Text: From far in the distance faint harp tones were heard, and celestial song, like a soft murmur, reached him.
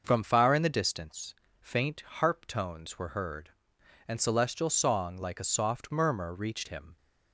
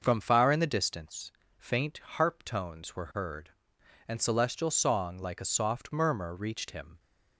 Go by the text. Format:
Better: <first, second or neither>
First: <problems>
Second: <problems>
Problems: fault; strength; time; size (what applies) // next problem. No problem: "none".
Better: neither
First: starts louder than the rest; noticeable; until 1.0 s; 6 dB // pauses between "distance" and "faint"; slight; at 1.3 s; 0.26 s long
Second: starts louder than the rest; until 1.0 s; 6 dB // pauses between "distance" and "faint"; slight; at 1.3 s; 0.26 s long